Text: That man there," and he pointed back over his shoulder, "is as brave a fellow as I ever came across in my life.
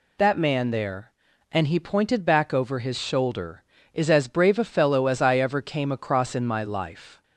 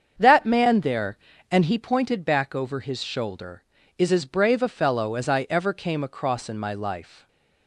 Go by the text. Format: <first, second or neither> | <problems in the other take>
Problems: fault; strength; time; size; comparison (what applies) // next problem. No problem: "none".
first | starts louder than the rest; strong; until 1.8 s; 7.5 dB // stays silent after the last word; slight; from 7.1 s on; 0.5 s long